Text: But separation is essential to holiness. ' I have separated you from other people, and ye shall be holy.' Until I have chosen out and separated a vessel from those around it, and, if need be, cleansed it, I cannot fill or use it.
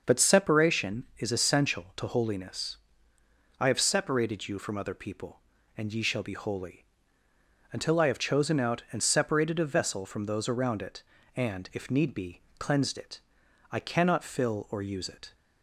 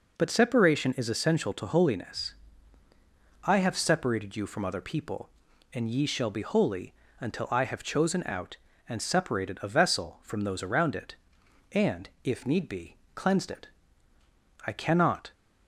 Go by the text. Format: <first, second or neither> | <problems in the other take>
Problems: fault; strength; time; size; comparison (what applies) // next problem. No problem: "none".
first | stops before "fill or use it"; at 15.3 s